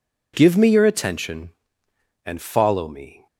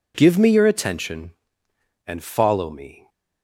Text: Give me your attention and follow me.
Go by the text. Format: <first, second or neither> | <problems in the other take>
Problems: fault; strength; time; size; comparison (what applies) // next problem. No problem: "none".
neither | none